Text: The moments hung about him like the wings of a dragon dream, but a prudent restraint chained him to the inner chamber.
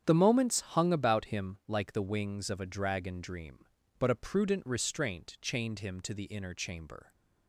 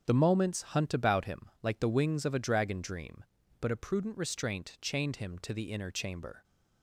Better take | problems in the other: first | starts louder than the rest; strong; until 1.1 s; 8 dB; strong in the first // says "hunt" for "hung"; at 0.6 s

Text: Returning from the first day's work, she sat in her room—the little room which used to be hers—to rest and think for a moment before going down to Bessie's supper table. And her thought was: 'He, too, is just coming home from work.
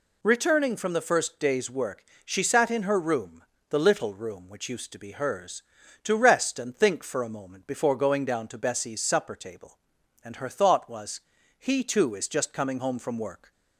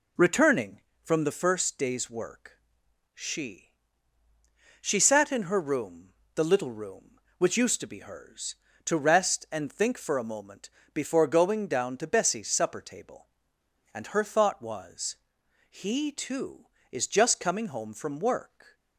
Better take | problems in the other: first | says "she" twice; at 4.8 s // pauses between "moment" and "before"; slight; at 10.7 s; 0.24 s long

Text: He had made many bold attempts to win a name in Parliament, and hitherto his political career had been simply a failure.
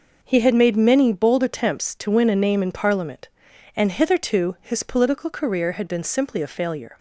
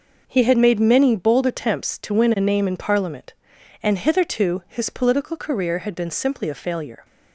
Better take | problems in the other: neither | none

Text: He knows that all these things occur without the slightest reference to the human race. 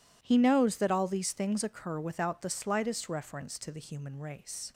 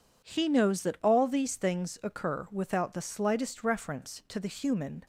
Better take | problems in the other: first | stops before "race"; at 5.0 s

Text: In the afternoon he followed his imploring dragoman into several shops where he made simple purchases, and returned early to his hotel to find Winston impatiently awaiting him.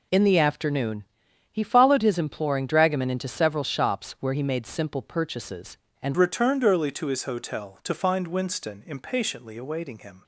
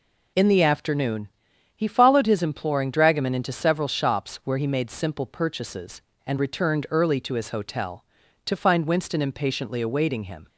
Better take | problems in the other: second | pauses between "afternoon" and "he"; noticeable; at 1.0 s; 0.48 s long; noticeable in the second // changes voice at "returned"; from 6.1 s on; 4.1 s long

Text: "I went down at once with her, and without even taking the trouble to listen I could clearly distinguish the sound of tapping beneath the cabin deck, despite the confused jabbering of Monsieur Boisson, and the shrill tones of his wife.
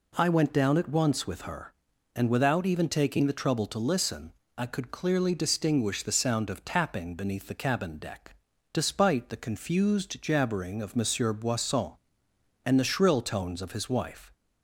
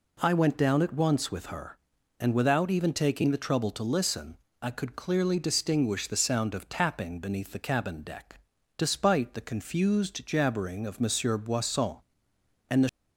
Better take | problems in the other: first | pauses between "listen" and "I"; slight; at 4.3 s; 0.24 s long; slight in the first // stops before "shrill tones of his wife"; at 12.8 s

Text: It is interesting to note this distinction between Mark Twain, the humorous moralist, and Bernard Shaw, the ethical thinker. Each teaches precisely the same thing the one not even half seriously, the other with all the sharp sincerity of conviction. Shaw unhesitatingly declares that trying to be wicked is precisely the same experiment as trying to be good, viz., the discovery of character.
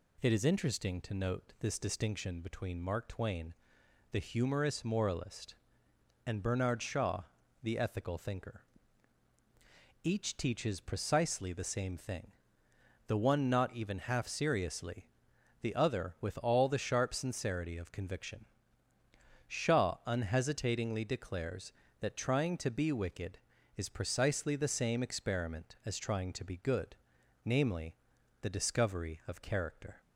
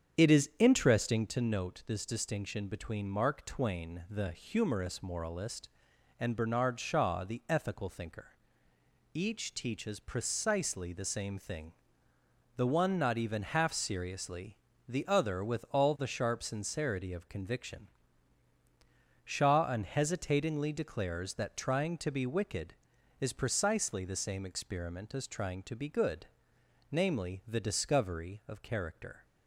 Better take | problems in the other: first | starts louder than the rest; strong; until 1.4 s; 8 dB // pauses between "thing" and "the"; noticeable; at 11.7 s; 0.86 s long; noticeable in the first

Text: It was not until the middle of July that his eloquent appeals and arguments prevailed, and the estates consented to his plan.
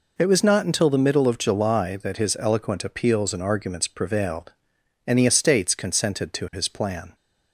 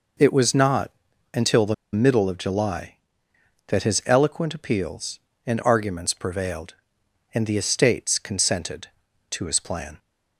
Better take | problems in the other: first | pauses between "not" and "until"; at 0.9 s; 0.42 s long // pauses between "the" and "middle"; slight; at 1.7 s; 0.19 s long

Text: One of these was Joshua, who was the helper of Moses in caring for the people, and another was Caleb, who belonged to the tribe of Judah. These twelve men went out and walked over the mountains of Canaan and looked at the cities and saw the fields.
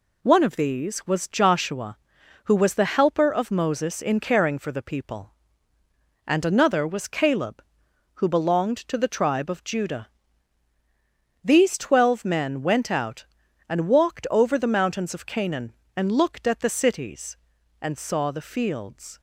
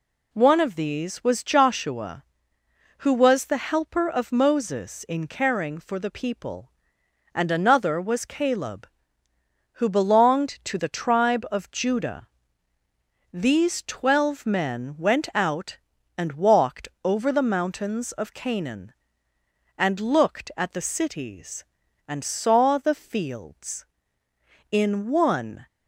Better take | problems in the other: first | pauses between "walked" and "over"; slight; at 16.8 s; 0.16 s long // goes on to say "In one"; noticeable; from 24.6 s on; 0.96 s long

